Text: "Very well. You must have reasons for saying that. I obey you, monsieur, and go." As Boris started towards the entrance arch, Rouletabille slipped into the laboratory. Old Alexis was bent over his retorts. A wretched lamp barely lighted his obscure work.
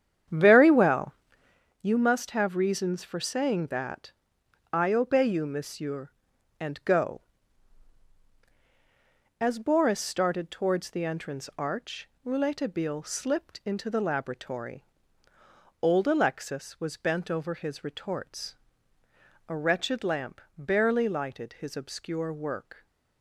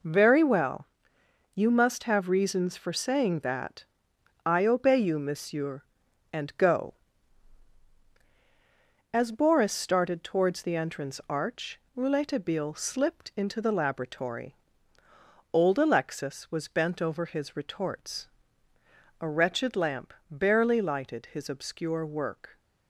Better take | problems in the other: second | starts louder than the rest; strong; until 1.7 s; 9 dB // pauses between "lamp" and "barely"; slight; at 20.4 s; 0.17 s long; slight in the second

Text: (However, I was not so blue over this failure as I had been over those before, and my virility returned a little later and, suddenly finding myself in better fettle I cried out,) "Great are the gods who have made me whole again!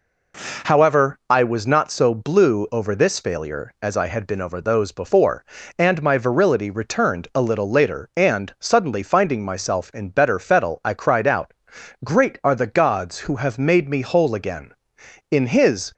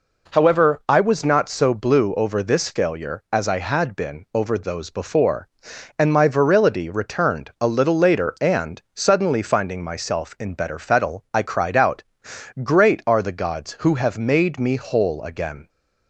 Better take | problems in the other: second | goes on to say "In his"; noticeable; from 15.3 s on; 0.62 s long

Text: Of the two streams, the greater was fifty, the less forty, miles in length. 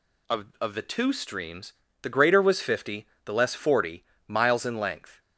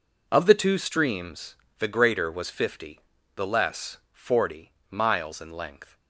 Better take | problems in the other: second | says "Of" twice; at 0.5 s

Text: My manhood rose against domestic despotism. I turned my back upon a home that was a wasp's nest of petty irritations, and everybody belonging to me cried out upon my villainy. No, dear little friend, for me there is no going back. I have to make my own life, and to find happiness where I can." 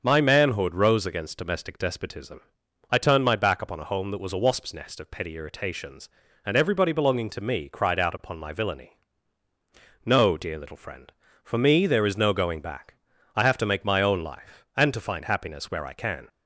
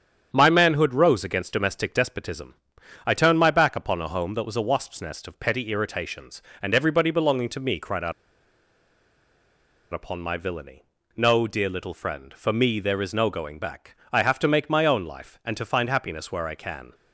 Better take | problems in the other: first | starts louder than the rest; strong; until 1.3 s; 8.5 dB; strong in the first // pauses between "out" and "upon"; strong; at 8.1 s; 1.8 s long

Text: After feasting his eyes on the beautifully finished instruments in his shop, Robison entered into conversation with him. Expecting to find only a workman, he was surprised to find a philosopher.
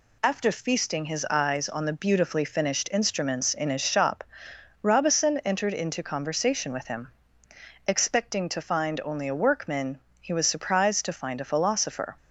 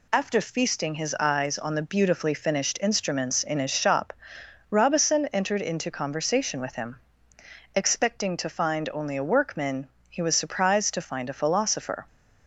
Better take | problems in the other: neither | none

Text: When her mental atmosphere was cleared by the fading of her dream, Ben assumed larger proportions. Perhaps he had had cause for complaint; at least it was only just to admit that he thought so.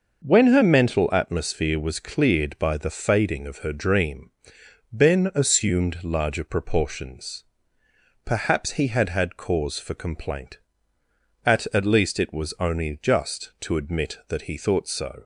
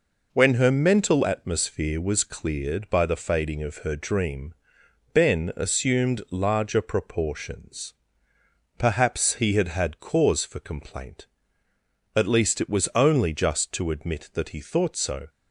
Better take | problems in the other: second | says "at" twice; at 11.7 s

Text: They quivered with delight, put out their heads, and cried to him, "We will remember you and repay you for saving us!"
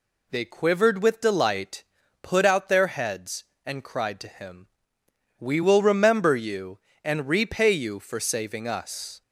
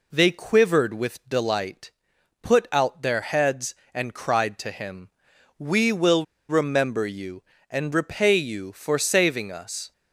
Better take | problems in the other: first | pauses between "will" and "remember"; slight; at 6.2 s; 0.24 s long

